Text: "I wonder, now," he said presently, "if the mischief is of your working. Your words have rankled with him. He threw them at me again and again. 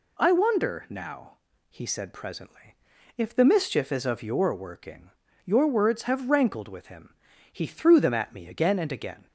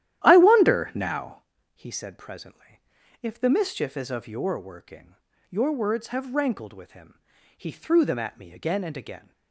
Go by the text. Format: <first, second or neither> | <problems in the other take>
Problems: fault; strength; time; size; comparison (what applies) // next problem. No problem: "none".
first | starts louder than the rest; strong; until 1.5 s; 12 dB